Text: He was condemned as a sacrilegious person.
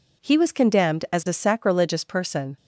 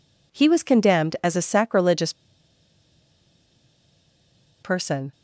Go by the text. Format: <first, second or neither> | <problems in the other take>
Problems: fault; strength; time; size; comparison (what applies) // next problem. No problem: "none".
first | pauses between "sacrilegious" and "person"; strong; at 2.1 s; 2.4 s long